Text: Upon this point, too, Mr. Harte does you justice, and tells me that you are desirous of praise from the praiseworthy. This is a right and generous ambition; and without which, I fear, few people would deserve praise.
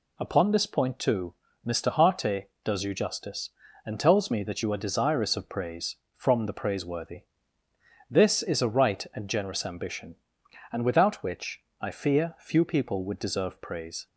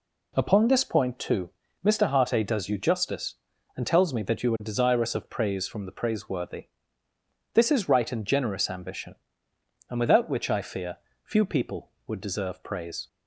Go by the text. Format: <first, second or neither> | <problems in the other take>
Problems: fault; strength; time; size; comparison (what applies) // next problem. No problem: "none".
first | skips "a"; at 7.8 s